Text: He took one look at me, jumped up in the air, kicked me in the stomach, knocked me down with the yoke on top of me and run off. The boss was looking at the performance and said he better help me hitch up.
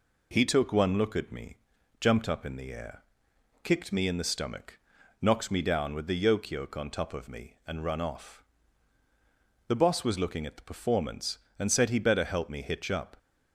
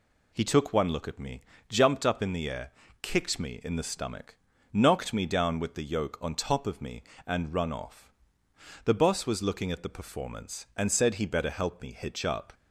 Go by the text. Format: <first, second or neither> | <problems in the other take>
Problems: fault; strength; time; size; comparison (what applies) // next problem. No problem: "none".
second | says "yoke" twice; at 6.4 s